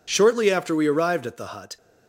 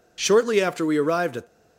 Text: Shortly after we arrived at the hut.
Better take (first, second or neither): first